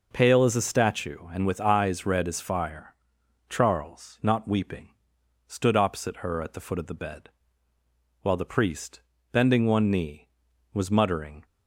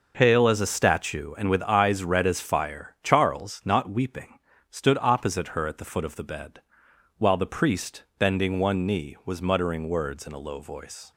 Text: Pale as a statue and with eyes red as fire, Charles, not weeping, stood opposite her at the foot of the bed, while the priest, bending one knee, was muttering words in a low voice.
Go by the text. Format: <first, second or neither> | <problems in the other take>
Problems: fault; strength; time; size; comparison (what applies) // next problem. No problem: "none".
second | stops before "words in a low voice"; at 11.4 s